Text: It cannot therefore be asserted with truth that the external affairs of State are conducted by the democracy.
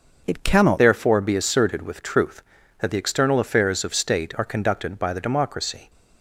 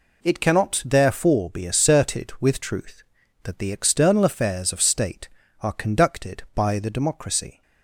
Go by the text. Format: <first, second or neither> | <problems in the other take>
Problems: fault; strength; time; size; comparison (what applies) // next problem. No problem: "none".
second | starts louder than the rest; until 1.2 s; 6 dB // changes voice at "therefore"; from 0.7 s on; 5.1 s long